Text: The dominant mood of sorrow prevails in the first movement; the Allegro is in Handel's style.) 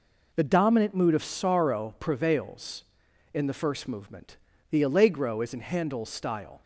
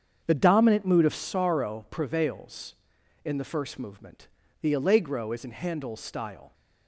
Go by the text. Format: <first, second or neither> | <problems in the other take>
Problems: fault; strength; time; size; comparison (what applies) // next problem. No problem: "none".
first | starts louder than the rest; strong; until 1.4 s; 7.5 dB